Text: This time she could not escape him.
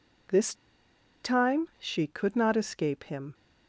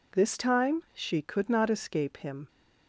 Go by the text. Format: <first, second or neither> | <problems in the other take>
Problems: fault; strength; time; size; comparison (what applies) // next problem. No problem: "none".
second | pauses between "This" and "time"; noticeable; at 0.5 s; 0.68 s long